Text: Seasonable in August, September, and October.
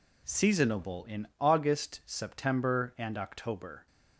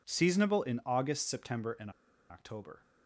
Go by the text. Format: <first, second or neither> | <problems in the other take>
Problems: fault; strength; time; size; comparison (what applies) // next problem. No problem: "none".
first | pauses between "and" and "October"; at 1.8 s; 0.40 s long